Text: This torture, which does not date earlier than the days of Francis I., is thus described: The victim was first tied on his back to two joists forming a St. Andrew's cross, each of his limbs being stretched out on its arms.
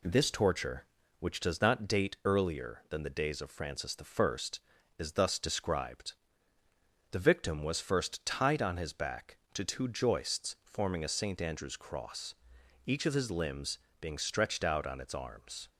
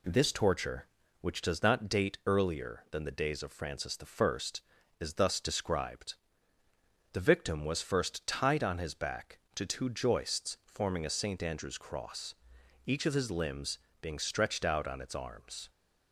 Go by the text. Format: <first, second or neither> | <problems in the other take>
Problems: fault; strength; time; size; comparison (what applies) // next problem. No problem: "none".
neither | pauses between "limbs" and "being"; slight; the same in both